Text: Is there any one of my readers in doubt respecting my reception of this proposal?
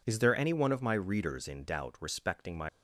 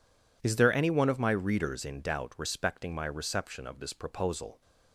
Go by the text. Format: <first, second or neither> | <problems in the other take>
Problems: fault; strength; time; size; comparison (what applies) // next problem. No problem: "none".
second | stops before "reception of this proposal"; at 2.6 s